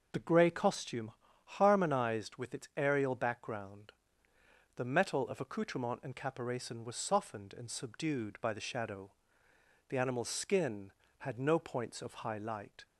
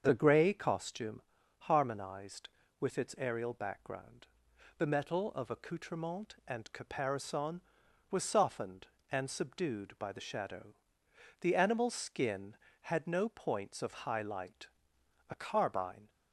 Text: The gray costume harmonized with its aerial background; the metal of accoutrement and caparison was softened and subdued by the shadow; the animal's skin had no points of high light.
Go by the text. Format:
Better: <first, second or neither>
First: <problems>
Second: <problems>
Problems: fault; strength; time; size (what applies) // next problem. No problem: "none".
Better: first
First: pauses between "costume" and "harmonized"; slight; at 1.1 s; 0.32 s long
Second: starts louder than the rest; until 1.0 s; 7 dB // pauses between "costume" and "harmonized"; at 1.2 s; 0.38 s long // goes on to say "A carbine"; noticeable; from 15.3 s on; 0.78 s long